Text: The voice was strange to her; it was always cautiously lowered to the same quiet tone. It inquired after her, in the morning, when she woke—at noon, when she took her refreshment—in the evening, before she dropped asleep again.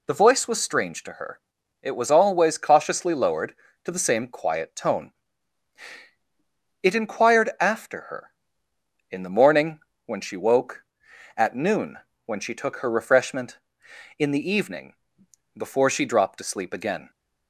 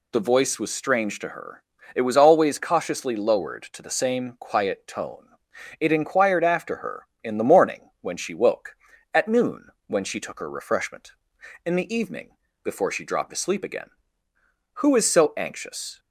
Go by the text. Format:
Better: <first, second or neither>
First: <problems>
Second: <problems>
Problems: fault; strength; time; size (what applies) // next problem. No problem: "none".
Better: first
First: none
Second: goes on to say "Who is so anxious"; noticeable; from 14.7 s on; 1.2 s long